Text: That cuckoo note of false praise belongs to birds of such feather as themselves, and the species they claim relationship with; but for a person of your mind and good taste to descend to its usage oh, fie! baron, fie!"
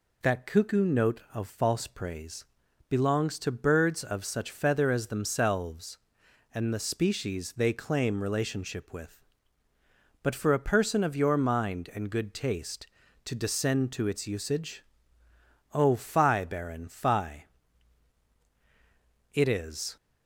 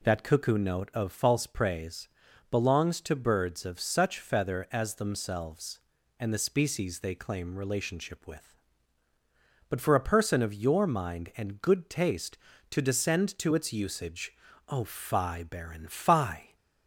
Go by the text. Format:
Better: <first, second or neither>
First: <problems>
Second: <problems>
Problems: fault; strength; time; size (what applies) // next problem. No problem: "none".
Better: second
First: pauses between "praise" and "belongs"; noticeable; at 2.4 s; 0.46 s long // pauses between "usage" and "oh"; noticeable; at 14.8 s; 0.90 s long // goes on to say "It is"; noticeable; from 19.3 s on; 0.64 s long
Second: pauses between "praise" and "belongs"; at 2.0 s; 0.42 s long // pauses between "usage" and "oh"; slight; at 14.3 s; 0.36 s long